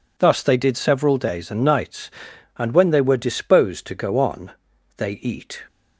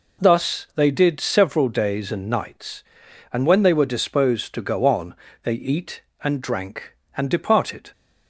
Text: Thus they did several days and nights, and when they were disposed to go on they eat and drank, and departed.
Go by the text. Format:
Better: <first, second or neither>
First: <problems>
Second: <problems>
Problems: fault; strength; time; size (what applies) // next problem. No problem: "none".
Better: second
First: pauses between "on" and "they"; at 4.5 s; 0.44 s long // stops before "and drank and departed"; at 5.6 s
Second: pauses between "on" and "they"; slight; at 5.1 s; 0.30 s long